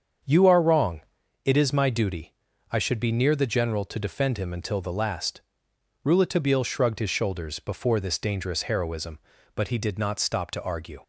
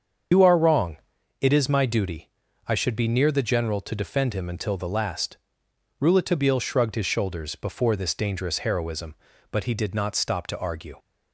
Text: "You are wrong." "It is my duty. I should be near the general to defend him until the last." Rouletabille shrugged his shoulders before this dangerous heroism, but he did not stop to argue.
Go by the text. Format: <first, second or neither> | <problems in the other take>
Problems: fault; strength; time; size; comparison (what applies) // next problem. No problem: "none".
first | loses the start of "You"; at 0.3 s; 110 ms // starts louder than the rest; strong; until 1.7 s; 7 dB; also in the first